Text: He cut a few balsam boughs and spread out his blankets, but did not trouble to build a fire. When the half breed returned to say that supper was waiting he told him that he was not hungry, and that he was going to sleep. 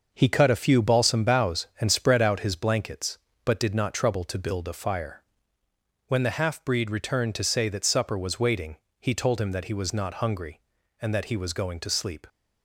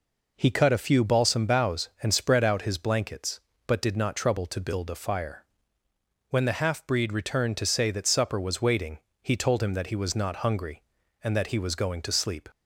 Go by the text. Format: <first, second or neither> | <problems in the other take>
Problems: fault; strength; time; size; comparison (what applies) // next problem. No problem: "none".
second | gets quieter; throughout; 6.5 dB // pauses between "waiting" and "he"; slight; at 8.7 s; 0.24 s long; slight in the second